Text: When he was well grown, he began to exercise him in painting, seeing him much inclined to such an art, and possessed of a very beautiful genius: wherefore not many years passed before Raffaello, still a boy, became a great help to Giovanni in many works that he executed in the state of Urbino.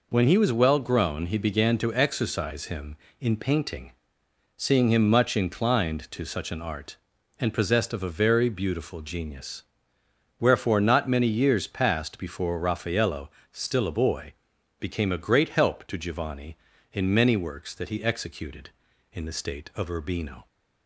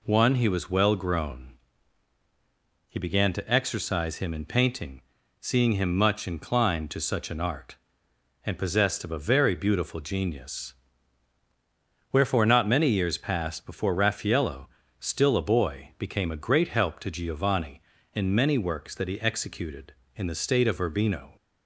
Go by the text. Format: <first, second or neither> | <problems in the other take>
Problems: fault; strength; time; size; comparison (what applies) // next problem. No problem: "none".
first | says "One" for "When"; at 0.0 s